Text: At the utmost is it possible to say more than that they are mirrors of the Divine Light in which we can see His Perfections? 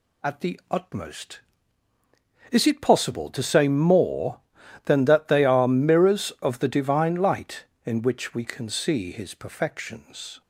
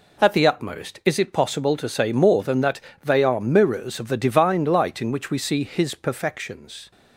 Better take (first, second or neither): first